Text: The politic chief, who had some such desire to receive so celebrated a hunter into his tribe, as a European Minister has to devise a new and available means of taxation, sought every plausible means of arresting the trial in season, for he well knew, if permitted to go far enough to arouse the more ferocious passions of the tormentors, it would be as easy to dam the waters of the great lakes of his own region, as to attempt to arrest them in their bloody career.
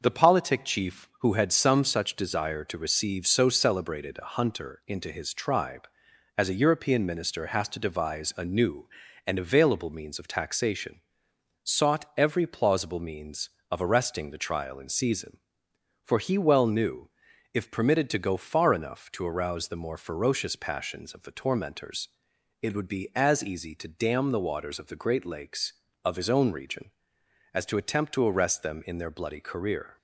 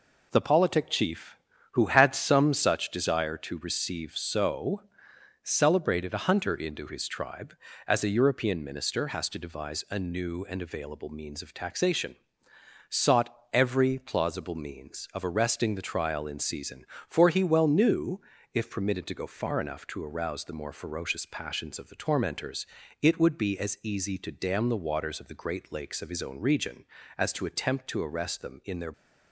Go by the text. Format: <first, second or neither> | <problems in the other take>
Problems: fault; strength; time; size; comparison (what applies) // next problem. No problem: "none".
first | pauses between "so" and "celebrated"; noticeable; at 4.8 s; 0.60 s long // pauses between "sought" and "every"; slight; at 13.3 s; 0.20 s long // stops before "bloody career"; at 28.9 s